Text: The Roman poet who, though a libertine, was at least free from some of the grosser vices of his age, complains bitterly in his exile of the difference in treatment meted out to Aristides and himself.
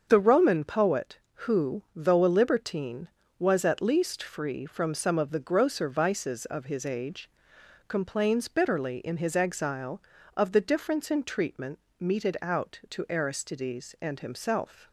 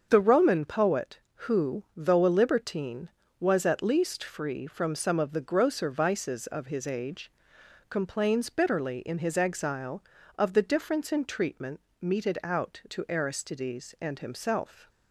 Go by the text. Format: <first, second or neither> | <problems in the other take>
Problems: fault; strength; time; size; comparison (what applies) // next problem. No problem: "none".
neither | starts louder than the rest; strong; the same in both // pauses between "treatment" and "meted"; slight; the same in both